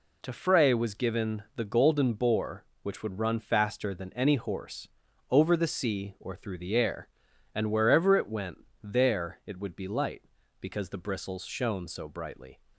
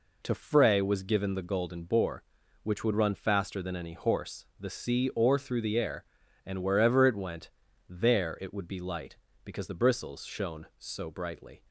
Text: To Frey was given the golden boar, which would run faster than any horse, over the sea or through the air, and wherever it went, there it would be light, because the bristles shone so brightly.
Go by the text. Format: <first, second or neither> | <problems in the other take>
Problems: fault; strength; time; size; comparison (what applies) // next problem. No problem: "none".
first | skips "over"; at 4.5 s